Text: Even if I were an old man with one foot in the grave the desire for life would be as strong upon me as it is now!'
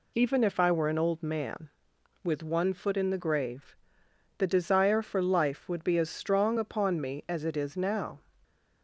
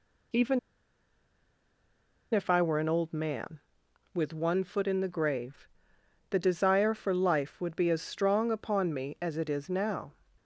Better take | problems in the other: first | pauses between "Even" and "if"; strong; at 0.5 s; 1.7 s long // pauses between "grave" and "the"; noticeable; at 5.6 s; 0.62 s long; noticeable in the first

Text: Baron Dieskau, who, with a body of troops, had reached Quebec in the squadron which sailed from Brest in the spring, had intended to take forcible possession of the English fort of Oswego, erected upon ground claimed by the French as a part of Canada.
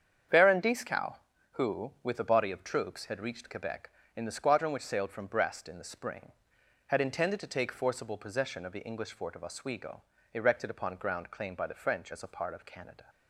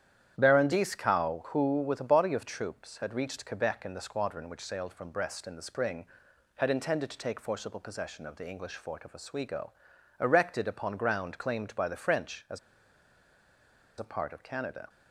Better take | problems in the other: first | starts louder than the rest; strong; until 1.3 s; 10 dB; strong in the first // pauses between "as" and "a"; strong; at 12.5 s; 1.4 s long

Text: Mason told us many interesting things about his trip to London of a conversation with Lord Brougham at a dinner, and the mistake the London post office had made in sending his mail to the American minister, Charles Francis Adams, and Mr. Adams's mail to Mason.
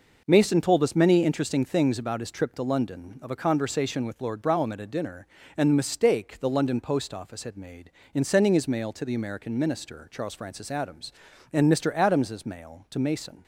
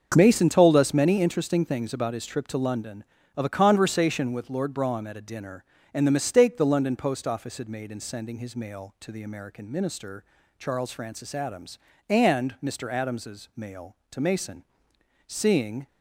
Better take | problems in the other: first | starts louder than the rest; until 1.1 s; 6.5 dB // goes on to say "Seeing"; from 15.2 s on; 0.60 s long

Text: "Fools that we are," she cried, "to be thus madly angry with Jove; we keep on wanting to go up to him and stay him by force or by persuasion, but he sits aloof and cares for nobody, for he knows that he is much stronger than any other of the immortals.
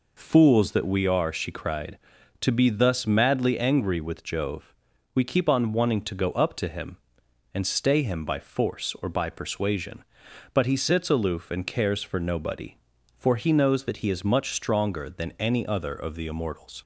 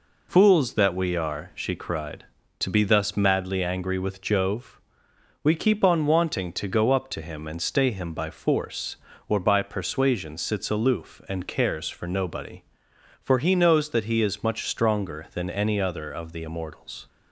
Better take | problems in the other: first | skips "but he"; at 10.3 s

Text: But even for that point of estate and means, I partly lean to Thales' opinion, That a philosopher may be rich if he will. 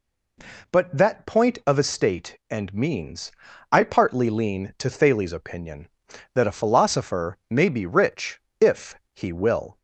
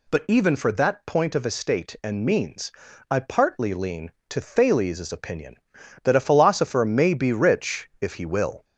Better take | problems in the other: second | skips "even for"; at 0.9 s // pauses between "rich" and "if"; slight; at 8.4 s; 0.20 s long // pauses between "if" and "he"; slight; at 8.9 s; 0.18 s long

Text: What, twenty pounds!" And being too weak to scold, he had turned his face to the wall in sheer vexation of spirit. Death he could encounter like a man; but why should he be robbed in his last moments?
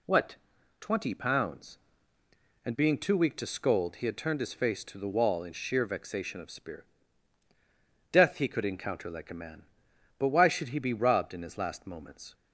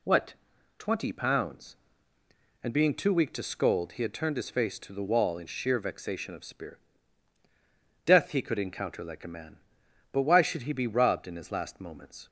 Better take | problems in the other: neither | none

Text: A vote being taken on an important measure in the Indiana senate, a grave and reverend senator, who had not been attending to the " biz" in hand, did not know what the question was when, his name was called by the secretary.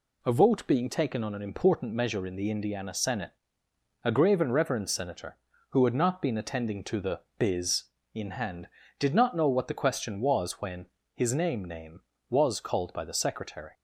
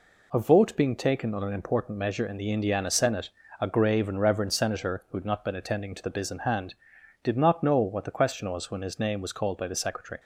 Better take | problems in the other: second | says "name" twice; at 11.6 s

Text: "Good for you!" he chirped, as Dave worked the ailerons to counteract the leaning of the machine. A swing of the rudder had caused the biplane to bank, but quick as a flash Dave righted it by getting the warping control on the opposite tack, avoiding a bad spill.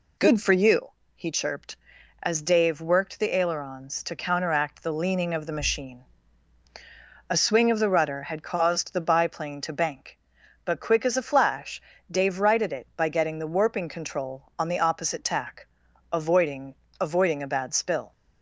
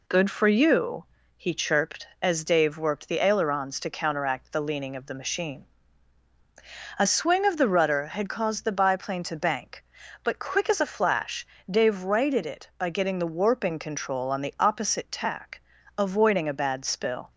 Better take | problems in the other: second | pauses between "flash" and "Dave"; slight; at 11.7 s; 0.30 s long; slight in the second // says "avoiding" twice; at 16.9 s

